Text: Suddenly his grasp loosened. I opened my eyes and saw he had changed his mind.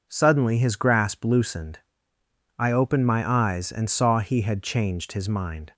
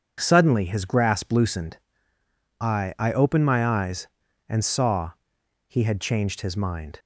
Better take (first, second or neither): first